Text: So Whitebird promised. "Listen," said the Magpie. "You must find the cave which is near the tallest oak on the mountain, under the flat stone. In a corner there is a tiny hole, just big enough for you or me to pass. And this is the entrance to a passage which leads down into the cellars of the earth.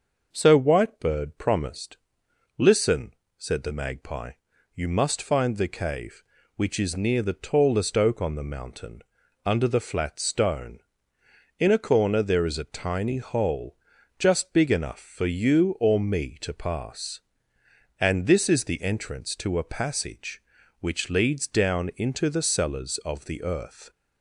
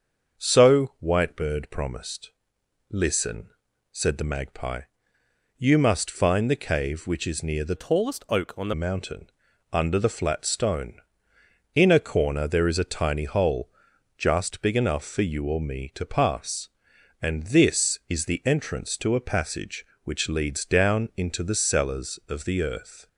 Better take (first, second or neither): first